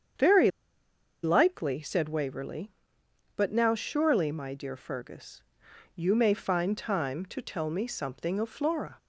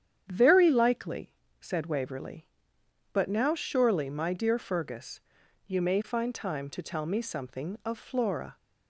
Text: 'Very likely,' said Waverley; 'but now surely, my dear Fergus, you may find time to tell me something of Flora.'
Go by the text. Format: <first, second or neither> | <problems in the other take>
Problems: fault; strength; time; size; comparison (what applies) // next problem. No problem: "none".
second | starts louder than the rest; strong; until 1.9 s; 7.5 dB; strong in the second // pauses between "Very" and "likely"; noticeable; at 0.4 s; 0.73 s long